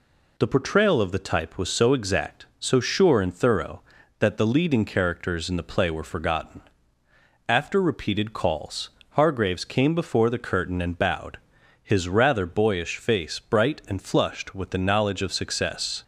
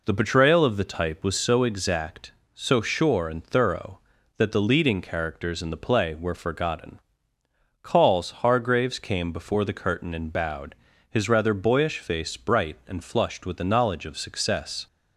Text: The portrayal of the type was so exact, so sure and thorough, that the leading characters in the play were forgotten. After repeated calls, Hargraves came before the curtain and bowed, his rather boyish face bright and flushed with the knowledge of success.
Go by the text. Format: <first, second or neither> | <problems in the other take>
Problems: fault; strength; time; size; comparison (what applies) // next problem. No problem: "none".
first | skips "After repeated"; at 7.3 s